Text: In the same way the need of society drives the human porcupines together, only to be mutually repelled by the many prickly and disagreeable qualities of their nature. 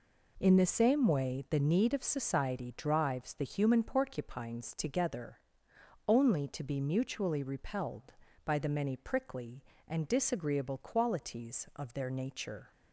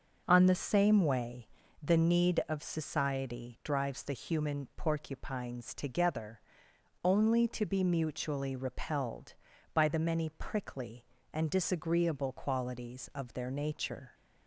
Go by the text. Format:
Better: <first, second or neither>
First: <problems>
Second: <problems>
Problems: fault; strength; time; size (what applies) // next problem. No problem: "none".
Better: first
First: none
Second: says "On" for "In"; at 0.2 s // pauses between "way" and "the"; slight; at 1.4 s; 0.34 s long